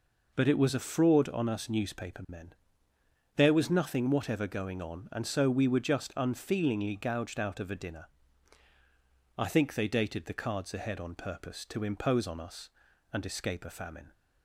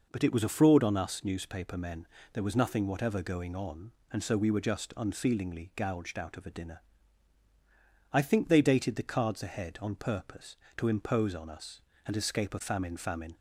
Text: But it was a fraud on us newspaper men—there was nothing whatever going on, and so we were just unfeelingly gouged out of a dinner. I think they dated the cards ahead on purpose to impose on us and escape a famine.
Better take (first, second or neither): first